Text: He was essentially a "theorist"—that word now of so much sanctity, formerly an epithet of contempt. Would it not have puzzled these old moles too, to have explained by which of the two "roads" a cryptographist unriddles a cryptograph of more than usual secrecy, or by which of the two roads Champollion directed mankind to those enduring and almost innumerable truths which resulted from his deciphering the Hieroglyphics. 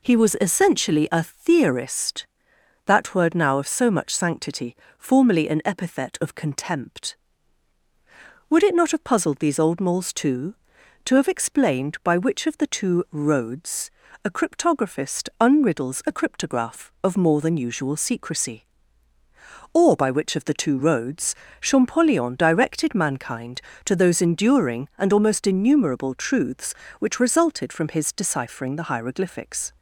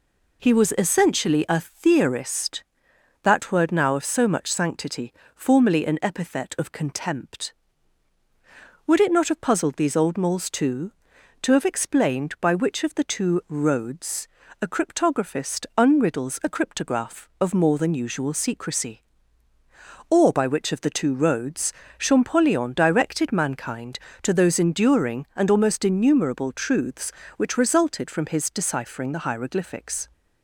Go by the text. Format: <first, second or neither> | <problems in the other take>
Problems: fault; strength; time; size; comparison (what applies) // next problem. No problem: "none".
neither | pauses between "roads" and "a"; slight; the same in both // pauses between "roads" and "Champollion"; slight; the same in both